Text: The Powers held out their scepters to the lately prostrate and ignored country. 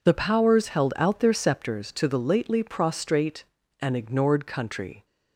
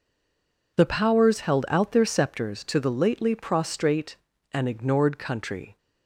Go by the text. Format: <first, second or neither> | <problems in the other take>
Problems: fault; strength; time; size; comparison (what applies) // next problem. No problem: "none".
first | stays silent before the first word; slight; until 0.7 s; 0.7 s long